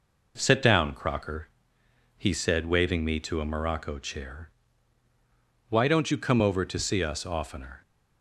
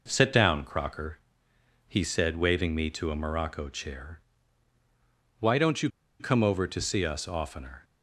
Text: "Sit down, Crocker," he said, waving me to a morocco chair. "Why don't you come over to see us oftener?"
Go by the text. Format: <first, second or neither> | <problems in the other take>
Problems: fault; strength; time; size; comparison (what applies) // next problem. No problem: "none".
first | pauses between "you" and "come"; slight; at 5.8 s; 0.31 s long